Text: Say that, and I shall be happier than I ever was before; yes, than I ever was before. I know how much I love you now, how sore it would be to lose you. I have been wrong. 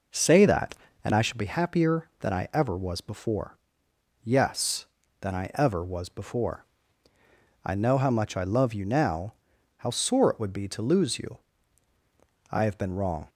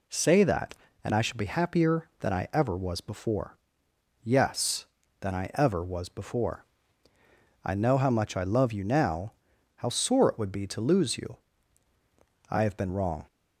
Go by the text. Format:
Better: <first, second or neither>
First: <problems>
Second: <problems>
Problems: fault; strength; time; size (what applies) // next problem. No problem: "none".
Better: second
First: starts louder than the rest; noticeable; until 1.4 s; 5 dB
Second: none